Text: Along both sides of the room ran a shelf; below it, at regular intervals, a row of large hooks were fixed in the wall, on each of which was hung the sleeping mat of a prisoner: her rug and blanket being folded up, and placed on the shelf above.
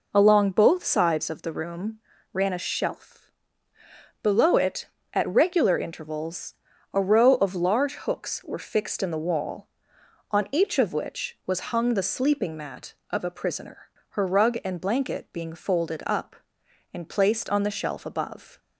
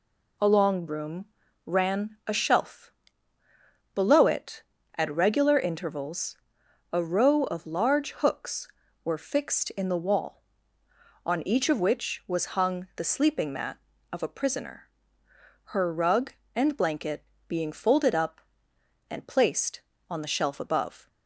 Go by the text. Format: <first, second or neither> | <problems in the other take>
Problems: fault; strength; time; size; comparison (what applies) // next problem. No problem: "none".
first | skips "both sides of the"; at 0.8 s // pauses between "room" and "ran"; at 1.2 s; 0.40 s long; slight in the first // pauses between "blanket" and "being"; slight; at 17.2 s; 0.24 s long